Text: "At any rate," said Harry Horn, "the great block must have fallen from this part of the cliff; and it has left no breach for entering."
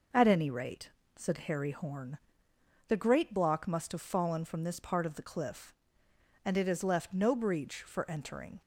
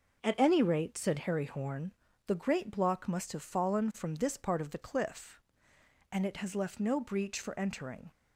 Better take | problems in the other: neither | none

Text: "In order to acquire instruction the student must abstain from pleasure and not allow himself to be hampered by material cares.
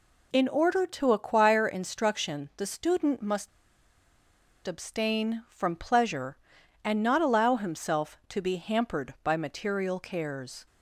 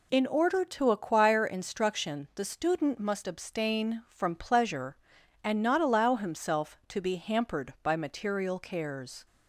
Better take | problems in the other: second | pauses between "must" and "abstain"; at 3.4 s; 1.1 s long

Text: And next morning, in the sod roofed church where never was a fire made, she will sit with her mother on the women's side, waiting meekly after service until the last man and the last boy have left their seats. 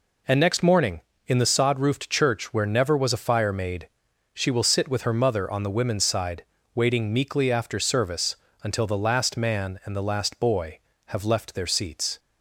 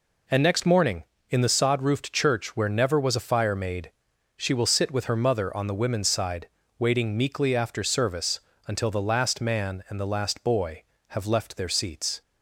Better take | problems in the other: neither | pauses between "service" and "until"; slight; the same in both

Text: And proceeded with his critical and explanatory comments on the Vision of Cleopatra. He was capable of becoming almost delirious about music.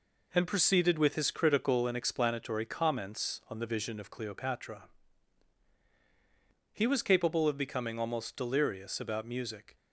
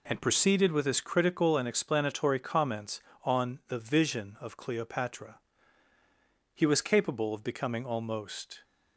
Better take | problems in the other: first | stops before "delirious about music"; at 8.6 s

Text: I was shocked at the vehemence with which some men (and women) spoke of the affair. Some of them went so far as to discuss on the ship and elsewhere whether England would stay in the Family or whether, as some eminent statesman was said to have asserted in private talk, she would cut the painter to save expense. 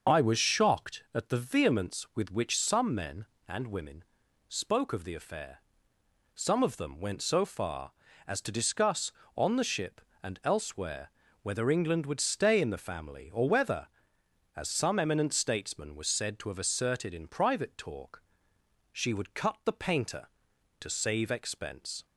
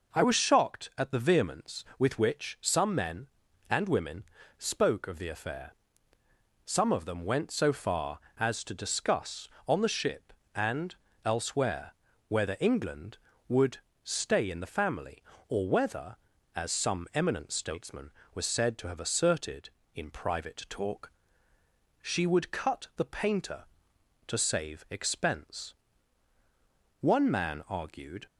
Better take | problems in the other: first | pauses between "and" and "elsewhere"; slight; at 10.9 s; 0.28 s long // pauses between "elsewhere" and "whether"; slight; at 11.9 s; 0.34 s long; slight in the first // pauses between "would" and "stay"; slight; at 13.7 s; 0.24 s long // goes on to say "One man argued"; noticeable; from 26.9 s on; 1.2 s long

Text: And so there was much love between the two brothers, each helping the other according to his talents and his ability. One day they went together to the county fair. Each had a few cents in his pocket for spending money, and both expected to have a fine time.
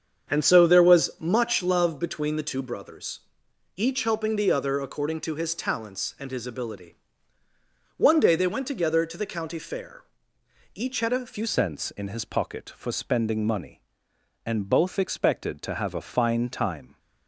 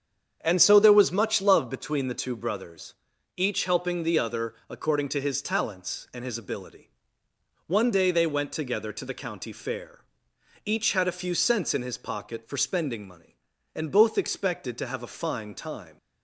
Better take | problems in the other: second | starts louder than the rest; strong; until 1.3 s; 7.5 dB; strong in the second // changes voice at "cents"; from 11.4 s on; 5.5 s long

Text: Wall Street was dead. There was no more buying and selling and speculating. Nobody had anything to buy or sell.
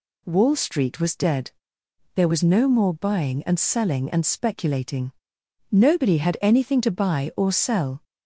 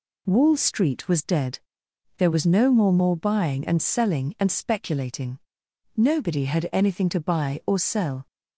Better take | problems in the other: first | says "more" twice; at 2.9 s

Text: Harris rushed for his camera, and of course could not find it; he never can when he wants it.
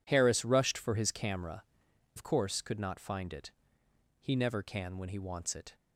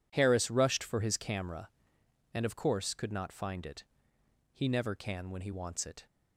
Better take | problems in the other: second | skips "and"; at 1.8 s

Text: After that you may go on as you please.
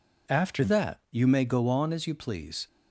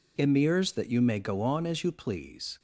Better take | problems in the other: first | says "Emirs" for "After"; at 0.1 s

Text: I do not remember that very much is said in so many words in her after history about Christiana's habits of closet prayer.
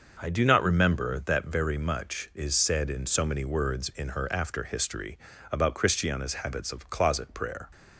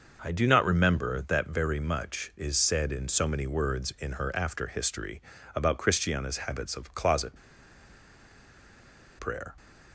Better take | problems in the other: first | starts louder than the rest; noticeable; until 1.2 s; 6 dB; noticeable in the first // pauses between "history" and "about"; slight; at 5.2 s; 0.34 s long; slight in the first // pauses between "closet" and "prayer"; strong; at 7.3 s; 1.8 s long

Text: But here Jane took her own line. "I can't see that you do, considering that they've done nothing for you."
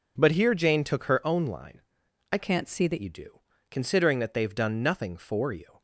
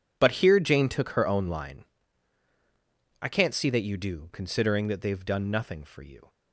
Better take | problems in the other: second | changes voice from "can't" to "that"; from 2.3 to 2.9 s; 0.6 s long

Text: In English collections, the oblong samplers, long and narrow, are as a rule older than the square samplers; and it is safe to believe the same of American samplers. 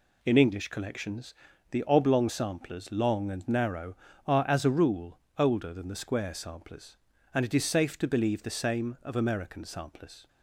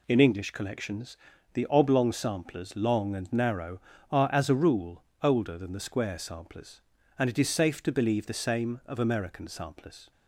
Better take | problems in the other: neither | pauses between "rule" and "older"; slight; the same in both

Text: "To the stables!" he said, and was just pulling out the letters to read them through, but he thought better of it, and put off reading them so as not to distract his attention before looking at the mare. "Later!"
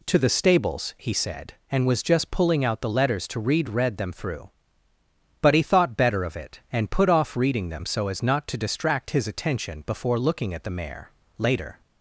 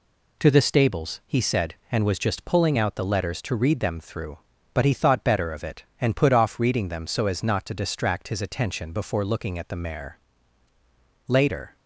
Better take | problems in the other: second | says "read" twice; at 3.6 s

